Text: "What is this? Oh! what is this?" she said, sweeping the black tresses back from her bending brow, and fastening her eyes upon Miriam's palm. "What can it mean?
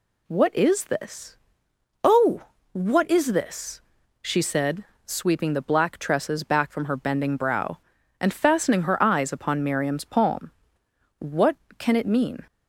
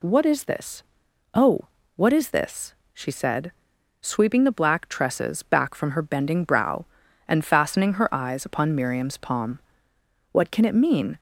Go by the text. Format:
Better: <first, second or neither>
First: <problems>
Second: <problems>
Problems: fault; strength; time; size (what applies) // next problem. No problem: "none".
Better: neither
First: none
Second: none